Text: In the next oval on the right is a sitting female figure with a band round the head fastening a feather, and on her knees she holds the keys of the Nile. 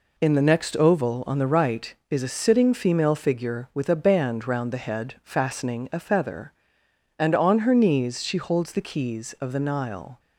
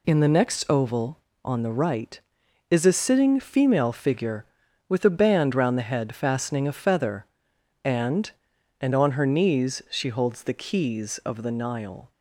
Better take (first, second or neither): first